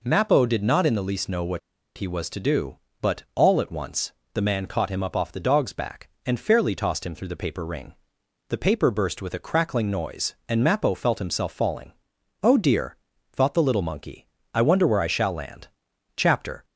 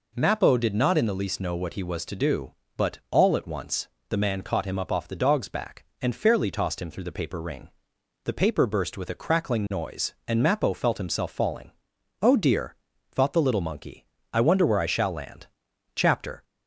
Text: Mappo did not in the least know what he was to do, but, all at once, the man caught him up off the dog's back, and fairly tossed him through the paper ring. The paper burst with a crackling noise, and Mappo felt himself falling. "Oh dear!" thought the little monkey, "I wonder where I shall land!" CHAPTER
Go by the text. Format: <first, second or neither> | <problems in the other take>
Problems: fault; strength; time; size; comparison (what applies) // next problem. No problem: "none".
second | pauses between "what" and "he"; at 1.5 s; 0.38 s long